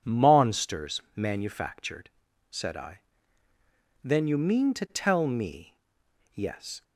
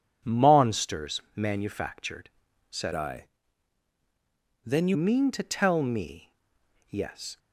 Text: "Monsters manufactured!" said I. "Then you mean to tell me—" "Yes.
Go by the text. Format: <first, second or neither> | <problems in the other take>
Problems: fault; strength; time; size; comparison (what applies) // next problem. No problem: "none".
first | changes voice from "I" to "you"; from 2.9 to 4.9 s; 2.0 s long